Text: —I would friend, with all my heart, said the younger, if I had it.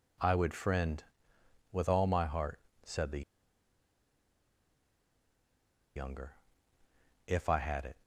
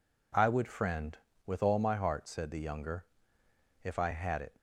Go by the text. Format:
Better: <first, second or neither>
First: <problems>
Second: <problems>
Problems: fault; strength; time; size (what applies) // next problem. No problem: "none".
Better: second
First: pauses between "the" and "younger"; strong; at 3.2 s; 2.7 s long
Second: none